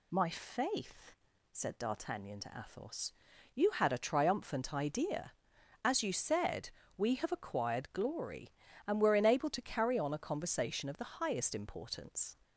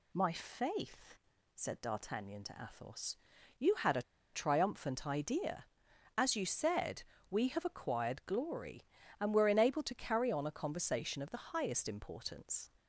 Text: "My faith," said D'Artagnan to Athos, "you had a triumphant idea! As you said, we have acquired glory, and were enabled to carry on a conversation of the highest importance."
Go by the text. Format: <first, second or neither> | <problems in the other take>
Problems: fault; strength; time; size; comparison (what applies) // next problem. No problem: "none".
first | pauses between "a" and "triumphant"; slight; at 4.0 s; 0.31 s long